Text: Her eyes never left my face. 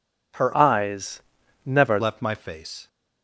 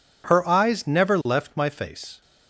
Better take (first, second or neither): second